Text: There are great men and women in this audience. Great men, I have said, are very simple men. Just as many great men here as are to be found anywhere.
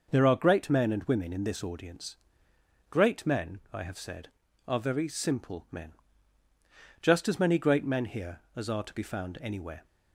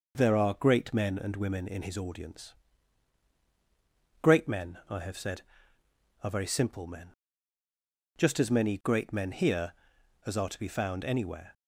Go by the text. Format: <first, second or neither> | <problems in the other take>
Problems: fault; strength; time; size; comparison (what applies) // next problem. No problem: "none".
first | says "his" for "this"; at 1.8 s